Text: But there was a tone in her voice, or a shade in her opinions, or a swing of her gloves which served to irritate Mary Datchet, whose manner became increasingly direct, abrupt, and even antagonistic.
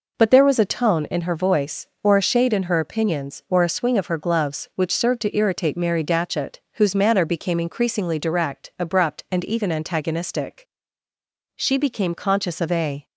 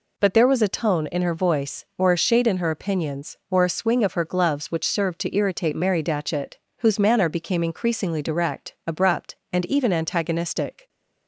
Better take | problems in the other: second | goes on to say "She became conscious of a"; from 11.5 s on; 1.5 s long

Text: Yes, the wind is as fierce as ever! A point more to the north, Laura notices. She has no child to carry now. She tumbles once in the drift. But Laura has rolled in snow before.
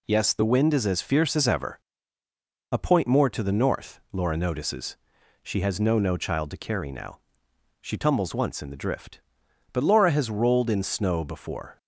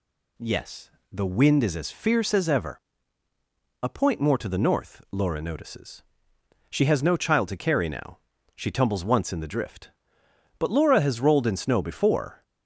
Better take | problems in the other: second | says "no" twice; at 5.9 s

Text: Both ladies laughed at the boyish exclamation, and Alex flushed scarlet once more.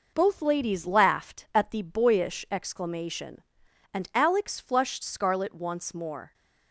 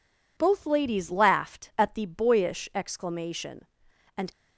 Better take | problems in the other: first | stops before "Alex flushed scarlet once more"; at 4.3 s

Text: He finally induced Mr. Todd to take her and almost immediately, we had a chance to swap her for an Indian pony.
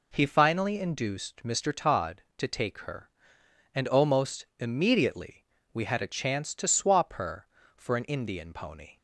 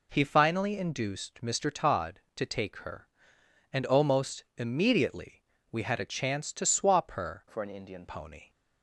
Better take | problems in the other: first | changes voice from "for" to "Indian"; from 7.4 to 8.0 s; 0.6 s long

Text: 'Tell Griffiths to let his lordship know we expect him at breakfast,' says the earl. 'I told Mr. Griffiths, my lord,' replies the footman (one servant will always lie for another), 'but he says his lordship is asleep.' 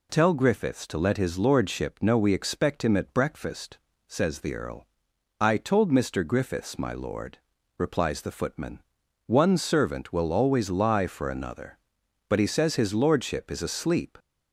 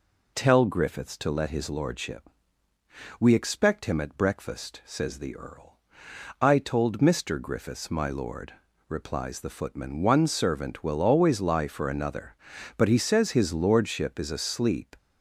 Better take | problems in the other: first | skips "know"; at 2.7 s

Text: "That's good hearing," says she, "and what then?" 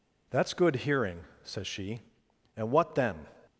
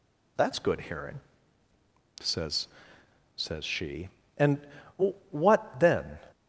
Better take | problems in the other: first | says "says" twice; at 3.3 s // pauses between "and" and "what"; noticeable; at 4.6 s; 0.70 s long

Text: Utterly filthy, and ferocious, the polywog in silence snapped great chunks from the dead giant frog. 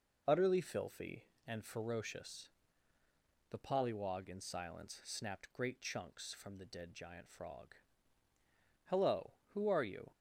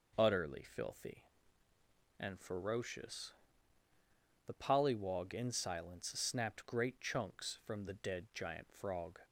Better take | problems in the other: second | goes on to say "Hello Who are you"; noticeable; from 8.9 s on; 1.2 s long

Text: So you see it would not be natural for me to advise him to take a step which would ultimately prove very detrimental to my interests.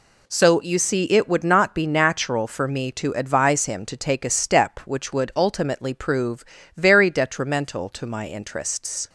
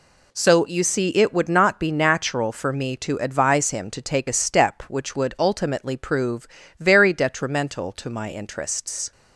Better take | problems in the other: neither | pauses between "prove" and "very"; slight; the same in both

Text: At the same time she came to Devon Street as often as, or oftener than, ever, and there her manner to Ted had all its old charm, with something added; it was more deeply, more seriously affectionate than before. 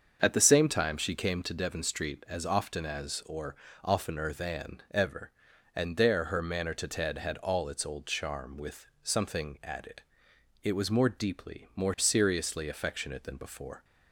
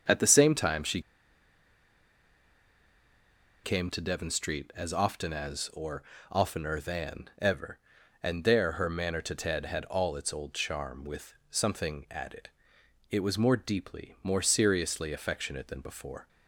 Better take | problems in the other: first | starts louder than the rest; until 3.7 s; 7 dB; also in the first // pauses between "she" and "came"; strong; at 1.0 s; 2.6 s long // pauses between "or" and "oftener"; slight; at 6.0 s; 0.28 s long; slight in the first // pauses between "with" and "something"; slight; at 11.3 s; 0.18 s long; slight in the first

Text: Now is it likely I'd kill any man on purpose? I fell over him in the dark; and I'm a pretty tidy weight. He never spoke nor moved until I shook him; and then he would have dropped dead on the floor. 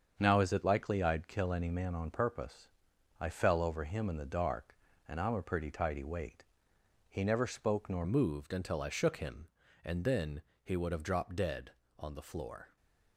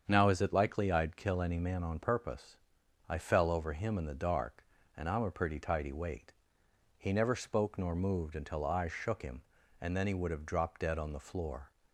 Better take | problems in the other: second | starts louder than the rest; until 1.1 s; 7 dB; strong in the second // changes voice at "moved"; from 8.0 s on; 4.7 s long // pauses between "then" and "he"; slight; at 10.4 s; 0.22 s long

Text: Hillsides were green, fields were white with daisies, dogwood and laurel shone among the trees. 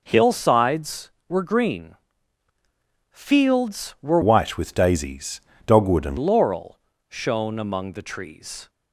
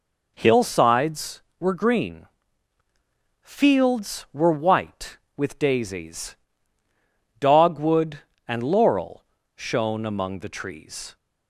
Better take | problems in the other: second | changes voice from "white" to "and"; from 4.2 to 6.1 s; 1.9 s long // pauses between "laurel" and "shone"; slight; at 6.7 s; 0.32 s long; slight in the second

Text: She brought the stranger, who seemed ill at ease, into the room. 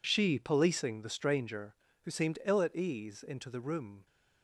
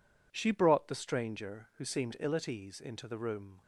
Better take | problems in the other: second | says "policing" for "brought"; at 0.3 s

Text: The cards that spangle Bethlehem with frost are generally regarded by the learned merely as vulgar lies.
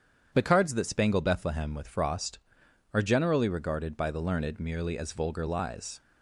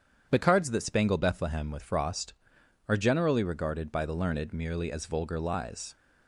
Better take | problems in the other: neither | starts louder than the rest; strong; the same in both

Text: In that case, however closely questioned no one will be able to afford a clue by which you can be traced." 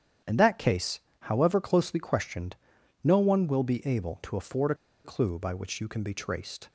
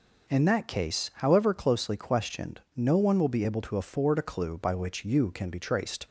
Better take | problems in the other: second | starts louder than the rest; strong; until 1.4 s; 9 dB // pauses between "questioned" and "no"; noticeable; at 2.5 s; 0.48 s long; slight in the second // pauses between "a" and "clue"; slight; at 4.7 s; 0.29 s long

